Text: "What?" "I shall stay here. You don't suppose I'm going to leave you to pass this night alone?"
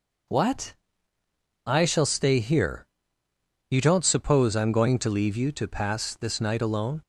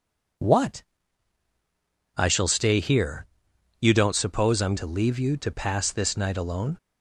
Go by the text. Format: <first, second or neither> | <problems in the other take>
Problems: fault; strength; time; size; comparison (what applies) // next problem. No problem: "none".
first | skips "going"; at 4.7 s